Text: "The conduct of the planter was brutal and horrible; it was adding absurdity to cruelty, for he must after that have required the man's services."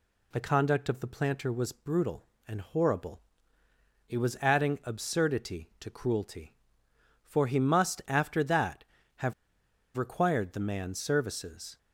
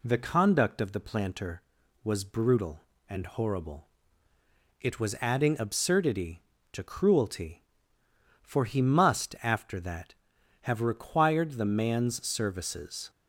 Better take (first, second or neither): second